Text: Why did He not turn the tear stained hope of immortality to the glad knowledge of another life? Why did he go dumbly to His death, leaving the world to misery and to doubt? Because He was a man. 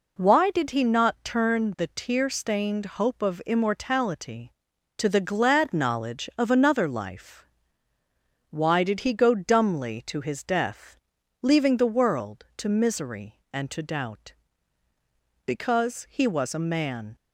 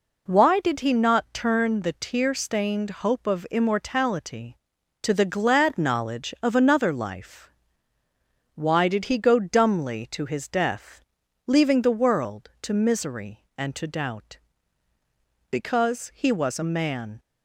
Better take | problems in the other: neither | pauses between "stained" and "hope"; slight; the same in both

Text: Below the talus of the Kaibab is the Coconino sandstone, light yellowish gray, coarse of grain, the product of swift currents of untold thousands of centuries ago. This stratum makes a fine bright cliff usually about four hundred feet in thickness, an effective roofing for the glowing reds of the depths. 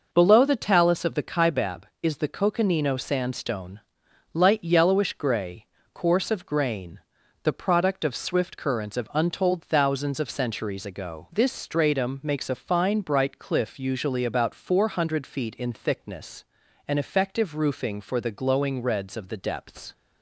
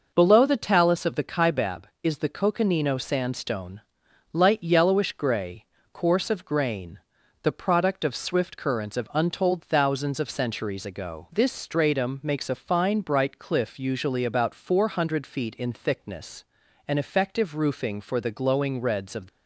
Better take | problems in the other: first | stops before "the depths"; at 19.2 s

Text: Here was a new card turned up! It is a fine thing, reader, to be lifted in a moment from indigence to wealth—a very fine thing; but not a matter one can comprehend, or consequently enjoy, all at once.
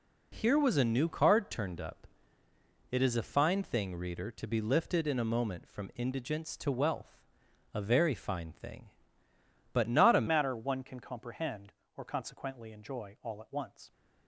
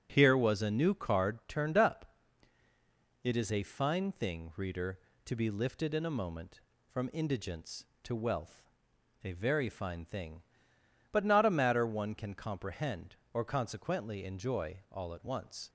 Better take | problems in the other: second | changes voice at "matter"; from 10.2 s on; 3.7 s long

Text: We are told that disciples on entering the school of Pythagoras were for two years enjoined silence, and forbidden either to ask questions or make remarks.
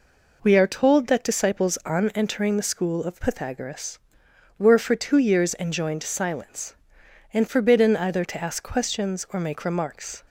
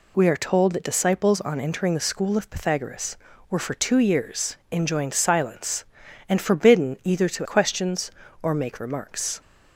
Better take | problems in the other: first | pauses between "years" and "enjoined"; slight; at 4.5 s; 0.16 s long // skips "ask"; at 7.4 s

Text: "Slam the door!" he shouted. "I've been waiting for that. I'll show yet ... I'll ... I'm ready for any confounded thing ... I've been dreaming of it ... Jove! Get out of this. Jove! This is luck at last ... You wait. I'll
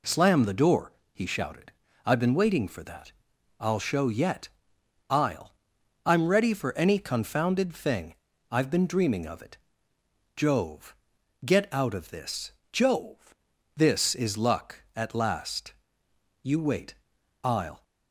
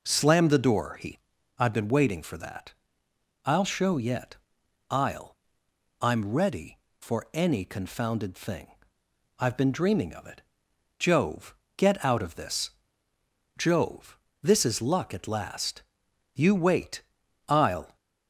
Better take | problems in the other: first | skips "shouted"; at 1.3 s

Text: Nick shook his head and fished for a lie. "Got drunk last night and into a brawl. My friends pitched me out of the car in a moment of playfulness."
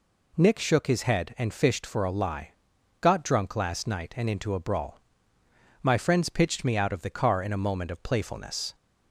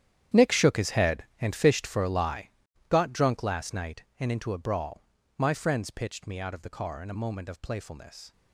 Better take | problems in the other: first | gets quieter; strong; throughout; 16 dB

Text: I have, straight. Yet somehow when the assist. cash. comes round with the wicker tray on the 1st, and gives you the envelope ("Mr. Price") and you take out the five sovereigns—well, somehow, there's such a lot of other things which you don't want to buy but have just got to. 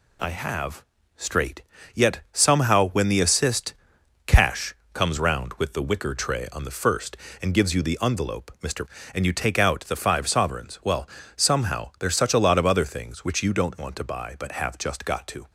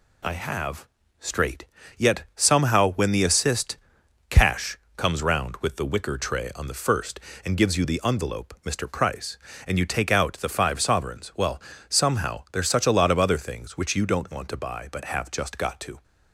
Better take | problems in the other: second | skips "Price"; at 8.9 s

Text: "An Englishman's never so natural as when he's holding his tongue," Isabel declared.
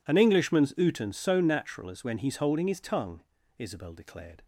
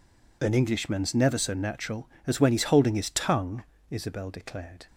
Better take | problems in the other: second | says "uten" for "never"; at 0.7 s

